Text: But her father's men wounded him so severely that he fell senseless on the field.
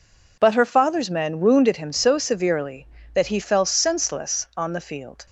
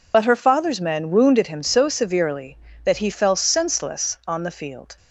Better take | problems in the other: first | loses the start of "But"; at 0.1 s; 45 ms

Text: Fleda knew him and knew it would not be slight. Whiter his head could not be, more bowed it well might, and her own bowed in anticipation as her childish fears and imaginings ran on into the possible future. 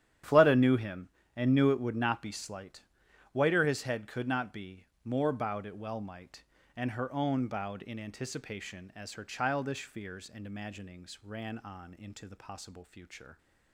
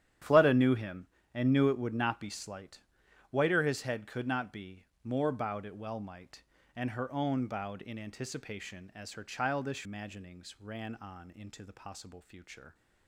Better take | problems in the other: first | starts louder than the rest; strong; until 1.5 s; 10.5 dB; strong in the first // skips "fears and"; at 9.8 s

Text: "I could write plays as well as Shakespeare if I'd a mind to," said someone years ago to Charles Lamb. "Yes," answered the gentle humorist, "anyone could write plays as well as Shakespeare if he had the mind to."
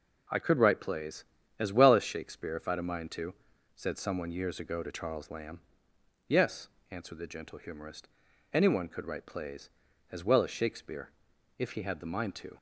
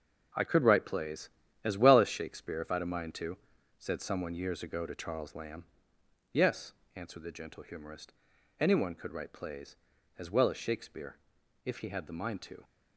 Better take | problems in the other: first | gets quieter; strong; throughout; 9 dB // pauses between "Shakespeare" and "if"; noticeable; at 11.1 s; 0.48 s long; noticeable in the first

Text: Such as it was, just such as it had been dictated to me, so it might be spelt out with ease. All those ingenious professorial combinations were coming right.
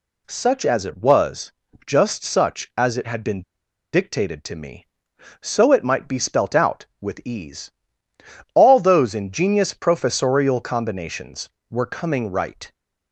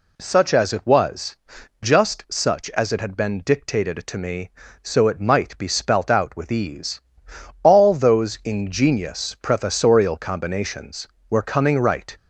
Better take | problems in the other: second | pauses between "been" and "dictated"; noticeable; at 3.4 s; 0.50 s long

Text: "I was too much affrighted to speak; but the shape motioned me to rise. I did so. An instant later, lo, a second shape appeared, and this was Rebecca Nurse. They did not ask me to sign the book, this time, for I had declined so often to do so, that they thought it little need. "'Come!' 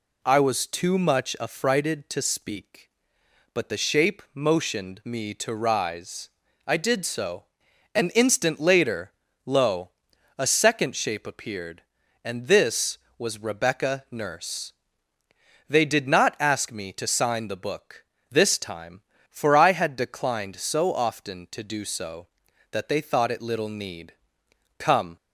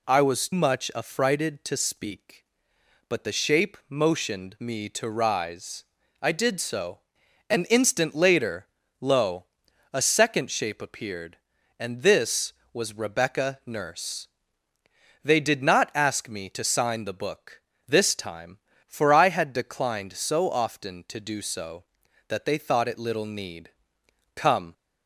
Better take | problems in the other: first | skips "too"; at 0.5 s

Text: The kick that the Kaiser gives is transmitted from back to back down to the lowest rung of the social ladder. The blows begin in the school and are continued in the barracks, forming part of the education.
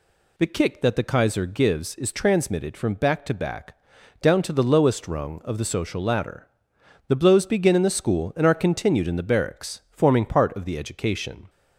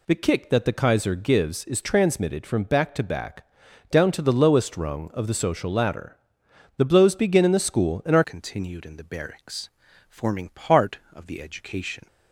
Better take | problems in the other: first | pauses between "back" and "down"; at 3.4 s; 0.42 s long; also in the first // changes voice at "continued"; from 8.2 s on; 3.8 s long

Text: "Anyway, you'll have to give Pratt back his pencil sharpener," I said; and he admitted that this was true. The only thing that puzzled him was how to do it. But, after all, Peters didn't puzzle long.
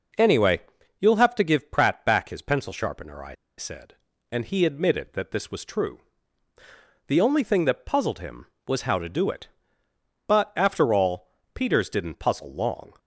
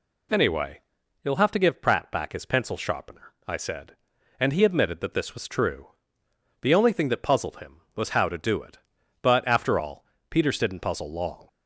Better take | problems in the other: second | pauses between "I" and "said"; slight; at 3.3 s; 0.24 s long

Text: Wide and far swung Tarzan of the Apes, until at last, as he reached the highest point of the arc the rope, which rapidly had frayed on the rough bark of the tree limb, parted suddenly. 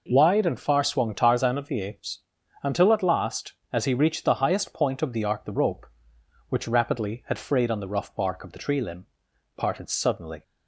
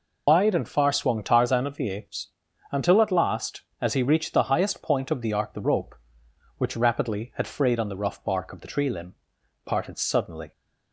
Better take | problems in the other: first | loses the start of "Wide"; at 0.2 s; 130 ms

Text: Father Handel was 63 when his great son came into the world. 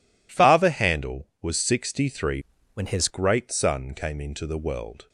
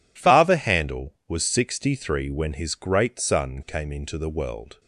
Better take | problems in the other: second | changes voice from "when" to "his"; from 2.7 to 3.0 s; 0.3 s long

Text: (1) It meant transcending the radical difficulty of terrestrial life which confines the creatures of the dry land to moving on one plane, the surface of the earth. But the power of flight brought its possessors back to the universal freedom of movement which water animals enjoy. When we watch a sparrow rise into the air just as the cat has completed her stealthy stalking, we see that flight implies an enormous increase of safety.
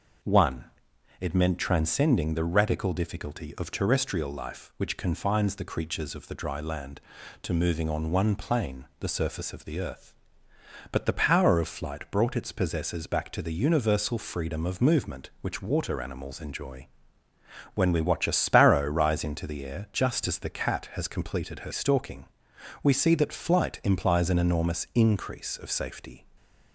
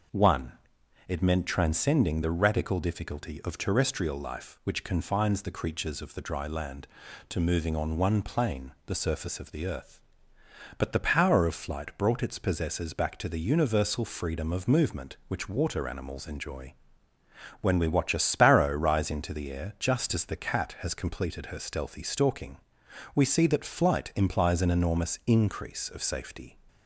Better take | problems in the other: second | starts louder than the rest; noticeable; until 1.7 s; 6 dB; also in the second // skips "stealthy"; at 21.7 s // stays silent after the last word; slight; from 26.1 s on; 0.6 s long

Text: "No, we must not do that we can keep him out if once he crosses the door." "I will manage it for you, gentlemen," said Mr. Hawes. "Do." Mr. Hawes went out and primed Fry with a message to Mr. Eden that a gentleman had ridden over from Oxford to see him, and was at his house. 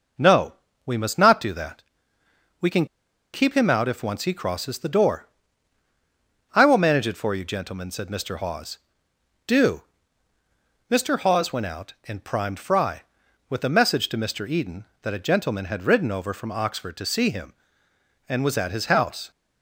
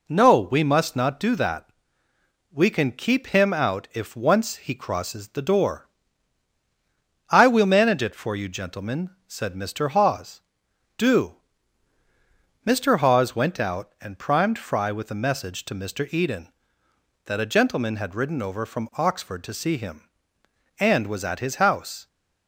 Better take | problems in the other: second | pauses between "that" and "we"; noticeable; at 1.8 s; 0.78 s long; noticeable in the second // pauses between "can" and "keep"; noticeable; at 2.8 s; 0.47 s long

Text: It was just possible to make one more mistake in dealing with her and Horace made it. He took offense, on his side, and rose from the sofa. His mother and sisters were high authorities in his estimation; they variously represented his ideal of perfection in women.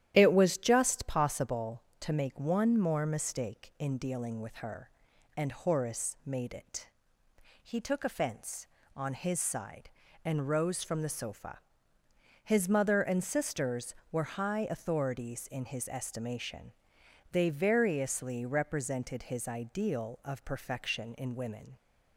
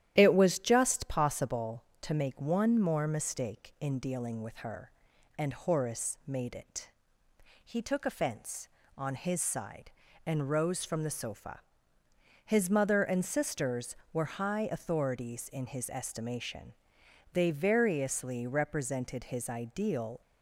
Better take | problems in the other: first | starts louder than the rest; strong; until 1.1 s; 11.5 dB; strong in the first // stops before "of perfection in women"; at 20.2 s

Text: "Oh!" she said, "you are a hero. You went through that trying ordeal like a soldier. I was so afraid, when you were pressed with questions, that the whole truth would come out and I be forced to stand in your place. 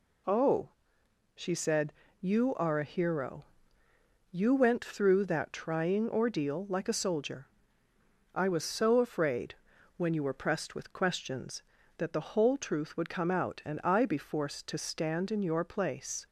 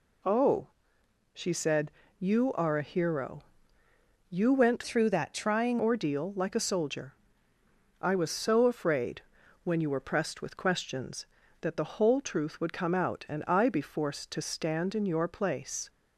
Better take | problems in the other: first | changes voice from "through" to "trying"; from 4.8 to 5.7 s; 0.9 s long

